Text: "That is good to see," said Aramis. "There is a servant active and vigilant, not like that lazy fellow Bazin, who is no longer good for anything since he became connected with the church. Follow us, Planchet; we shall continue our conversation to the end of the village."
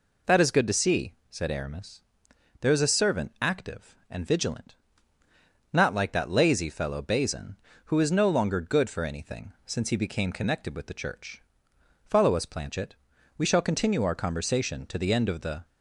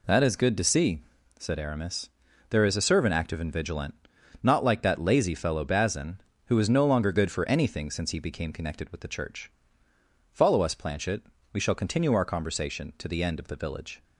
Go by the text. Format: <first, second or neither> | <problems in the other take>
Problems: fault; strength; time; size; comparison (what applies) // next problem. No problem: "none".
second | stops before "village"; at 15.6 s